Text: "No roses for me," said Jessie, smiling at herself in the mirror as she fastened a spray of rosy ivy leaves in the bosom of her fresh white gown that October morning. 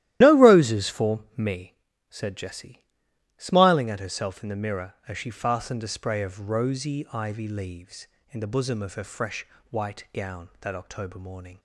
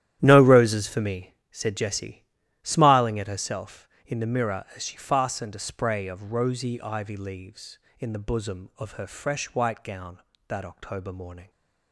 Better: second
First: loses the start of "No"; at 0.2 s; 30 ms // starts louder than the rest; strong; until 1.2 s; 14 dB // pauses between "fresh" and "white"; slight; at 9.4 s; 0.26 s long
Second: starts louder than the rest; strong; until 1.2 s; 12 dB

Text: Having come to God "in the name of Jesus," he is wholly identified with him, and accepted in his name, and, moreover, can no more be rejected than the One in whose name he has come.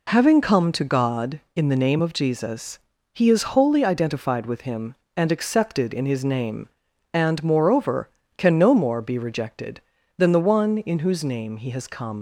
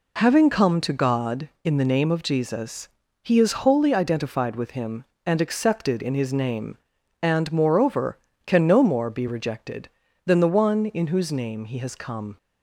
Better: second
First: leaves "come" unfinished; at 12.1 s; 75 ms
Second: none

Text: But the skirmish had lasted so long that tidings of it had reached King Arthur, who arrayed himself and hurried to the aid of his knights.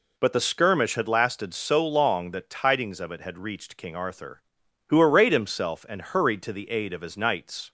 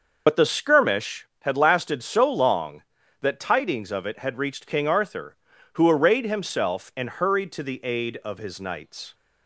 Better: first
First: none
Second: loses the start of "But"; at 0.2 s; 45 ms

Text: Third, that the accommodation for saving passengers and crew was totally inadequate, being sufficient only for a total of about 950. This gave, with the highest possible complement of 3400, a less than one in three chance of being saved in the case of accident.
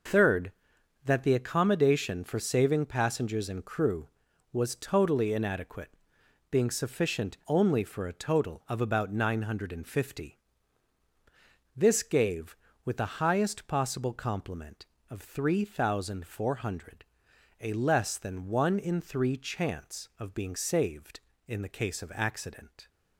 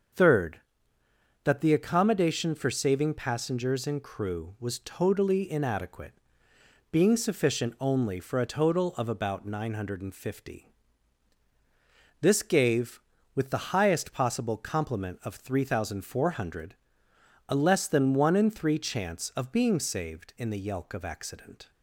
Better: first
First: none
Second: starts louder than the rest; until 2.0 s; 7 dB // says "yelk" for "case"; at 20.5 s

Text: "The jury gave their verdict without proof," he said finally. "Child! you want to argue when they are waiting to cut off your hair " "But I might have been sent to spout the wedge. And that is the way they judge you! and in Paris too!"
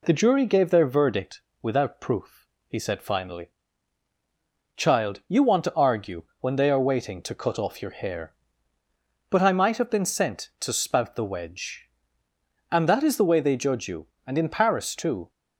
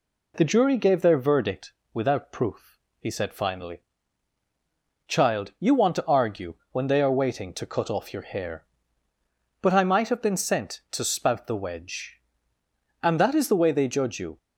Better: first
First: pauses between "verdict" and "without"; slight; at 1.3 s; 0.22 s long // pauses between "argue" and "when"; slight; at 6.2 s; 0.18 s long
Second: pauses between "verdict" and "without"; slight; at 1.7 s; 0.22 s long // pauses between "argue" and "when"; slight; at 6.5 s; 0.18 s long // stops before "and in Paris too"; at 14.3 s

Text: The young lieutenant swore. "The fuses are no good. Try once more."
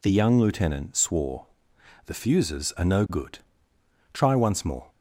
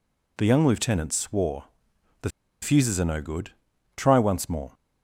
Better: first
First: none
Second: pauses between "The" and "fuses"; slight; at 2.2 s; 0.33 s long

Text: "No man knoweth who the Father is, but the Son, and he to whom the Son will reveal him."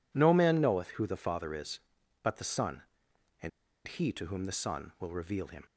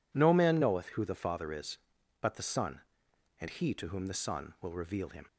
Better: second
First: pauses between "and" and "he"; at 3.5 s; 0.37 s long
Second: none

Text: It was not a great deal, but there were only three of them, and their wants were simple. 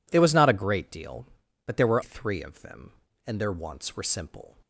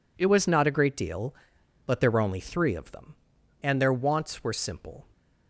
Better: second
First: skips "only"; at 2.0 s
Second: none

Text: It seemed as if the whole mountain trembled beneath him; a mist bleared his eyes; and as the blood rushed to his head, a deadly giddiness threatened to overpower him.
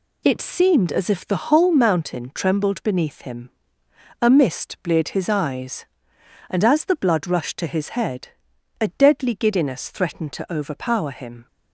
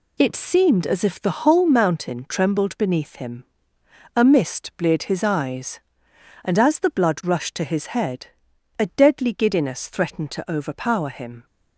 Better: neither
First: none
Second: none

